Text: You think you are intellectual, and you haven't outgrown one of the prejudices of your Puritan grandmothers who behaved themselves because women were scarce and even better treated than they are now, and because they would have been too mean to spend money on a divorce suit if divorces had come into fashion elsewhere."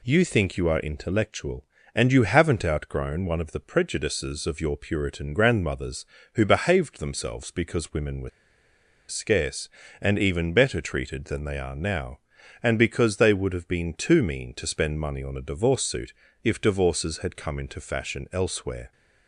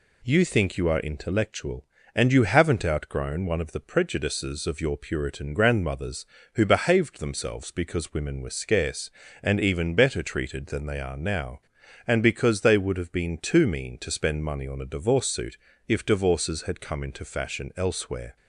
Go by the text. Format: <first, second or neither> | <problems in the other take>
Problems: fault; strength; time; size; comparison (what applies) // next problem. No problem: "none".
second | pauses between "were" and "scarce"; noticeable; at 8.2 s; 0.79 s long // pauses between "suit" and "if"; slight; at 16.1 s; 0.28 s long; slight in the second